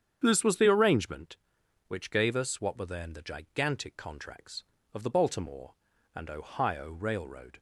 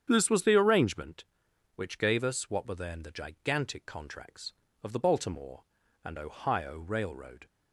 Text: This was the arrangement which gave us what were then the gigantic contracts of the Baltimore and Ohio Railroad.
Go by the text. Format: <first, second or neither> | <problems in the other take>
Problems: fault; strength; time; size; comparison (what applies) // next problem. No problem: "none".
neither | starts louder than the rest; strong; the same in both